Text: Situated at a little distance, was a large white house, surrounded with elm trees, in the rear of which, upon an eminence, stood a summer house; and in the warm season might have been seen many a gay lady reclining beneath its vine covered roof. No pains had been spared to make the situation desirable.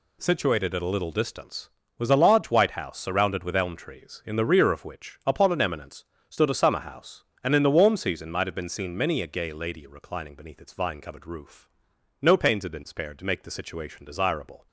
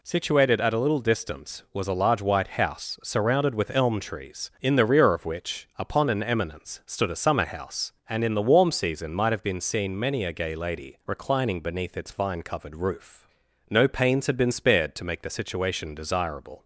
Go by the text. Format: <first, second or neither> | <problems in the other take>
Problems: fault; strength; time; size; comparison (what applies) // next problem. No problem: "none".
neither | none